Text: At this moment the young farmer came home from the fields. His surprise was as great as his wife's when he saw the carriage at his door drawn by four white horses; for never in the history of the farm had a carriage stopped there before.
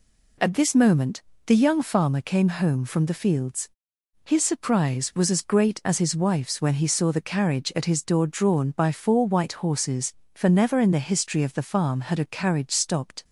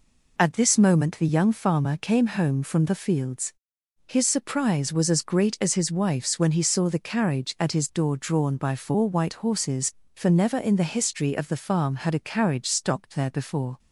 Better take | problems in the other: second | pauses between "moment" and "the"; slight; at 1.2 s; 0.26 s long // stops before "there before"; at 13.2 s

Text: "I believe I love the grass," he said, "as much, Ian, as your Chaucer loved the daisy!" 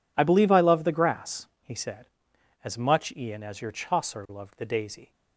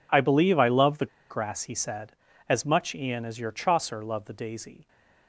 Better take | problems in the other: first | pauses between "the" and "grass"; slight; at 1.0 s; 0.24 s long

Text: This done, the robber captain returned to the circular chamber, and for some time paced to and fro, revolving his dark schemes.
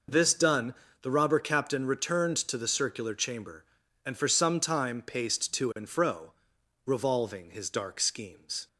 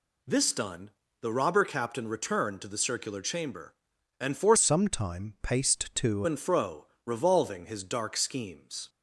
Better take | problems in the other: first | changes voice from "some" to "to"; from 4.5 to 6.2 s; 1.7 s long

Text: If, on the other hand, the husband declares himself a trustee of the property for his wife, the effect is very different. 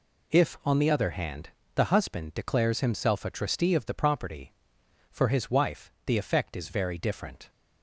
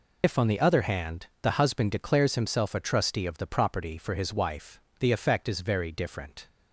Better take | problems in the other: first | loses the start of "If"; at 0.2 s; 75 ms

